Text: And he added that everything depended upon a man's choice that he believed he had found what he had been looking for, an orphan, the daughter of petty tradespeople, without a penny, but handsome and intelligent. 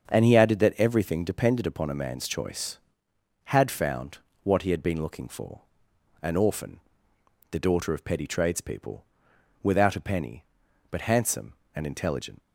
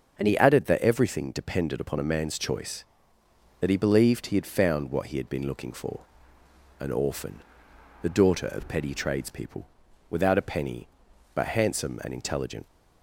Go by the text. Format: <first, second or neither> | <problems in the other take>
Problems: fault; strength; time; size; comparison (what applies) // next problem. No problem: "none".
second | starts louder than the rest; until 1.1 s; 6.5 dB; also in the second // skips "that he believed he"; at 3.1 s // pauses between "found" and "what"; slight; at 4.1 s; 0.24 s long